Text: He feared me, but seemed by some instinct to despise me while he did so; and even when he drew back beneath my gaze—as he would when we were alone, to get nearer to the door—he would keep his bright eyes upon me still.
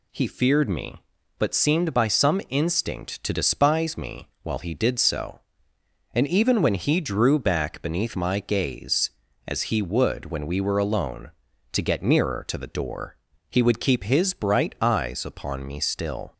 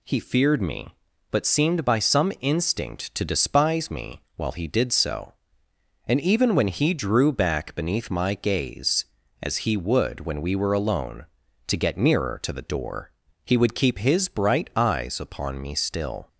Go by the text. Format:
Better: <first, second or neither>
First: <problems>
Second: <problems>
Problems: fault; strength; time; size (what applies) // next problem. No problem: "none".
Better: neither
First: pauses between "me" and "while"; slight; at 4.2 s; 0.16 s long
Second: pauses between "me" and "while"; slight; at 4.1 s; 0.16 s long